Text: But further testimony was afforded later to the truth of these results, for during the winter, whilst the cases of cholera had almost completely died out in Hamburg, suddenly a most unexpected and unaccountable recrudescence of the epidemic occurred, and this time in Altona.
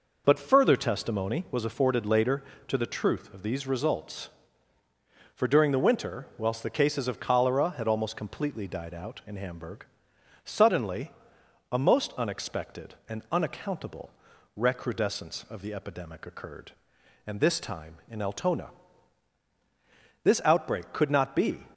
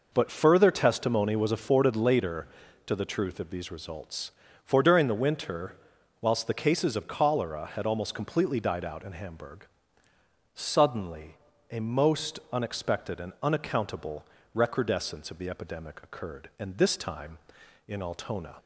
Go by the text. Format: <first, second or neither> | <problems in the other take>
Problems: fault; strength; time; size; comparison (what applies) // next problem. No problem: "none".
second | pauses between "suddenly" and "a"; noticeable; at 11.1 s; 0.58 s long; slight in the second // pauses between "unaccountable" and "recrudescence"; noticeable; at 14.0 s; 0.46 s long; slight in the second // goes on to say "This outbreak could not be"; from 20.2 s on; 1.4 s long